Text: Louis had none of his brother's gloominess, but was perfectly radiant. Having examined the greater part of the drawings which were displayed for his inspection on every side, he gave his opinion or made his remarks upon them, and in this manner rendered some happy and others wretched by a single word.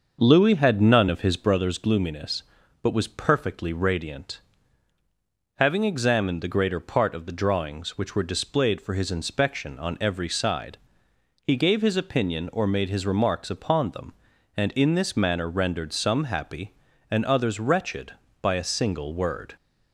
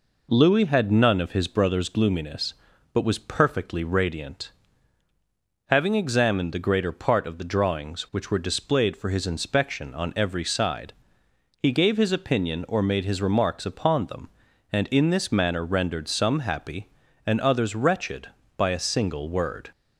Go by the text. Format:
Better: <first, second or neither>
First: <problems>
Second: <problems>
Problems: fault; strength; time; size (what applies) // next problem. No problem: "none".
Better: second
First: starts louder than the rest; until 1.6 s; 6 dB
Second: none